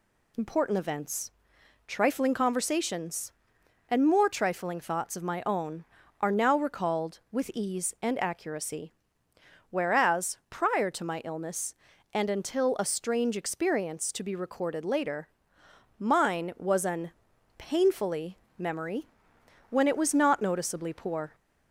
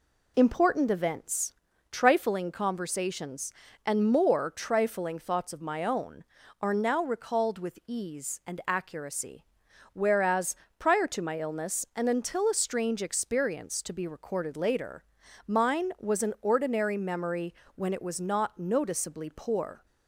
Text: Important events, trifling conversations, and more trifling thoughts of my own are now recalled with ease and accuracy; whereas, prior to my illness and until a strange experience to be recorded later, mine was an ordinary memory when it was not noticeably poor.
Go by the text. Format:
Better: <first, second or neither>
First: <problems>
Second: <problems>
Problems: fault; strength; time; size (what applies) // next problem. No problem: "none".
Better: second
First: says "painfully" for "ordinary"; at 17.5 s // pauses between "memory" and "when"; noticeable; at 19.0 s; 0.62 s long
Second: pauses between "memory" and "when"; slight; at 17.5 s; 0.22 s long